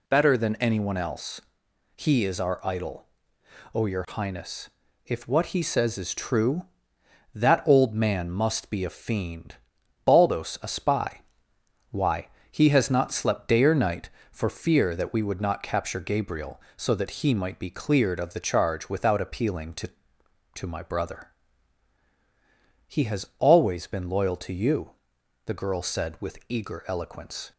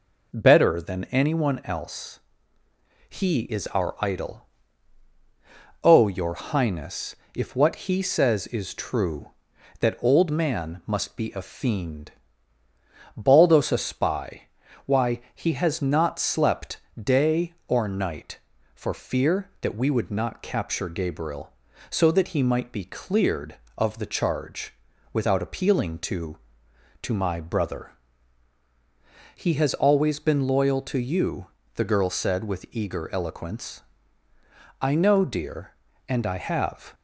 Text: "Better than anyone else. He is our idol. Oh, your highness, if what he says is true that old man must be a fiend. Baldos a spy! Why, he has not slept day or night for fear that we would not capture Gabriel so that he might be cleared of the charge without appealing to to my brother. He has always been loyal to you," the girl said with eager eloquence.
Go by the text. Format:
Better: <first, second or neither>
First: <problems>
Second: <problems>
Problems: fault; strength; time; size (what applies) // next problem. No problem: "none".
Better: first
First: none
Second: pauses between "slept" and "day"; slight; at 16.7 s; 0.24 s long // pauses between "charge" and "without"; at 24.7 s; 0.38 s long // goes on to say "I know dear and I have"; strong; from 34.8 s on; 2.1 s long